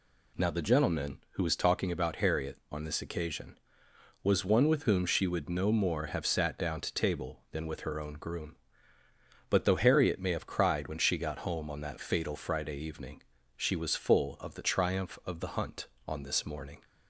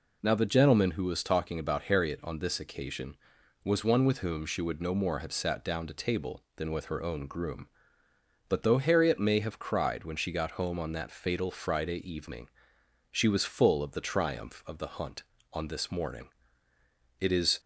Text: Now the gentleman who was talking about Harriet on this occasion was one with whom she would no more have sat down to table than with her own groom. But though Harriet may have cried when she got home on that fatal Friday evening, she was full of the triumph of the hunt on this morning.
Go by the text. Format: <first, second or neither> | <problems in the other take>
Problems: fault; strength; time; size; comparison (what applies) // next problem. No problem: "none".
first | goes on to say "It is"; slight; from 17.1 s on; 0.40 s long